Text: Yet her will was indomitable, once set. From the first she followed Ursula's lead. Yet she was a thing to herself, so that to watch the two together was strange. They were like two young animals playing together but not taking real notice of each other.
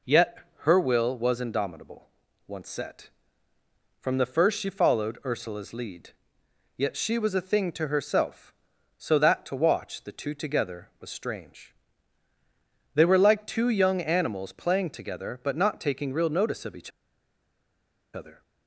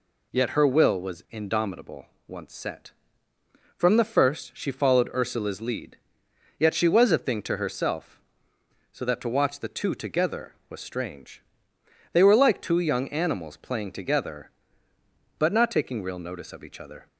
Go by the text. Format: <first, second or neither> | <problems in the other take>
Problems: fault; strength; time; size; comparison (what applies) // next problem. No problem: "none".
second | pauses between "Yet" and "her"; slight; at 0.3 s; 0.22 s long // pauses between "each" and "other"; strong; at 16.9 s; 1.2 s long